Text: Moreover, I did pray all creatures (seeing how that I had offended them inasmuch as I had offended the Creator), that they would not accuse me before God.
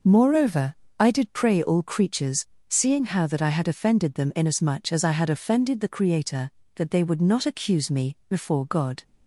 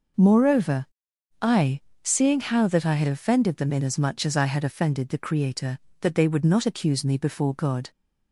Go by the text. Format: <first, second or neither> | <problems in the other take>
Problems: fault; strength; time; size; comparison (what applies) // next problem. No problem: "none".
first | skips "did pray all creatures"; at 1.9 s